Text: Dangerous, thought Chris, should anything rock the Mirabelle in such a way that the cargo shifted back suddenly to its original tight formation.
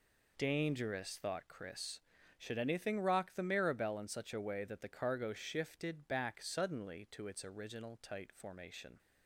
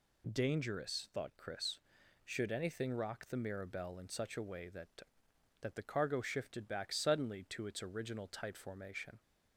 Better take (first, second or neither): first